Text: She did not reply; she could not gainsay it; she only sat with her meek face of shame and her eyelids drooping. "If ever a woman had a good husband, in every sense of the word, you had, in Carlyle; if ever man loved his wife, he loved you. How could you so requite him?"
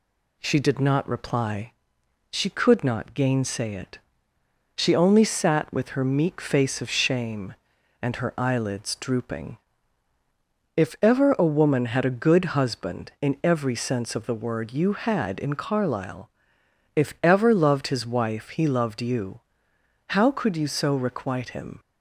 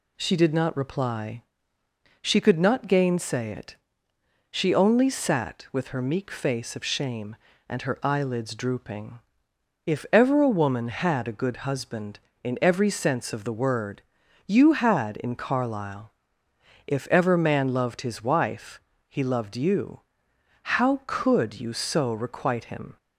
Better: second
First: skips "man"; at 17.5 s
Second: none

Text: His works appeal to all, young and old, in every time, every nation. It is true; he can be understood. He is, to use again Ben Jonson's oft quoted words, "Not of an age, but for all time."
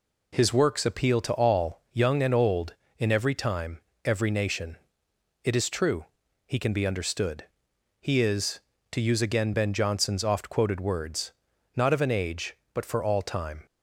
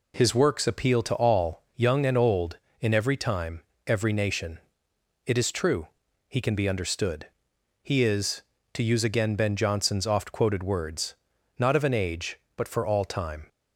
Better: neither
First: none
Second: none

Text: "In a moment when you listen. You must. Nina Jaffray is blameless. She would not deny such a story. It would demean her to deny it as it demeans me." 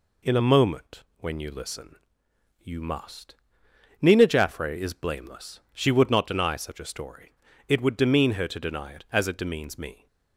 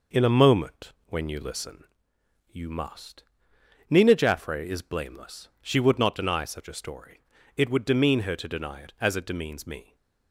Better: first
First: pauses between "moment" and "when"; slight; at 1.0 s; 0.16 s long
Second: starts louder than the rest; noticeable; until 1.9 s; 5 dB // pauses between "moment" and "when"; slight; at 0.9 s; 0.16 s long

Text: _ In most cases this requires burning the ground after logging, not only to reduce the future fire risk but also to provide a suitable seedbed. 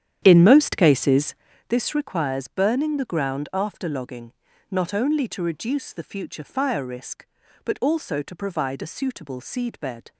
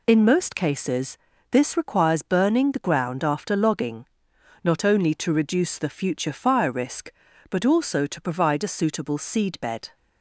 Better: second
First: starts louder than the rest; strong; until 1.8 s; 10 dB // pauses between "cases" and "this"; slight; at 1.3 s; 0.34 s long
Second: pauses between "cases" and "this"; slight; at 1.1 s; 0.34 s long

